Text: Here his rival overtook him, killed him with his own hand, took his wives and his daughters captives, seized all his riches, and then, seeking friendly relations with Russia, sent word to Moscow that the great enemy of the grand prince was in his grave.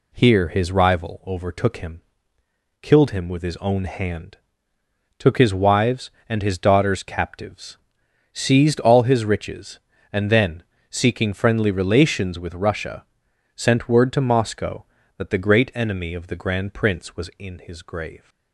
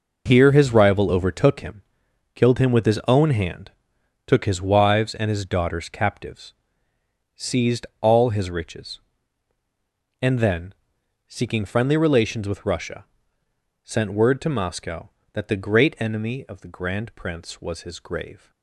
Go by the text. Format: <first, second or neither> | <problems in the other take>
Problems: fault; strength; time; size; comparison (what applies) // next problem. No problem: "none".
first | skips "in"; at 17.8 s